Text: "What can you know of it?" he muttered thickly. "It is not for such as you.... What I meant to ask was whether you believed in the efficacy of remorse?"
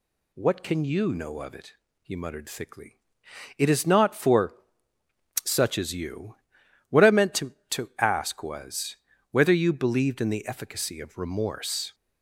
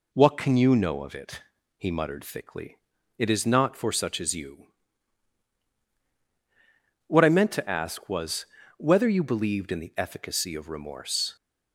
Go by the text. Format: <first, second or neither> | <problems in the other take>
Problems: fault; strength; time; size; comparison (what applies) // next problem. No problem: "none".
second | pauses between "for" and "such"; noticeable; at 4.5 s; 0.88 s long // says "to" twice; at 7.7 s // pauses between "was" and "whether"; at 8.9 s; 0.38 s long; slight in the second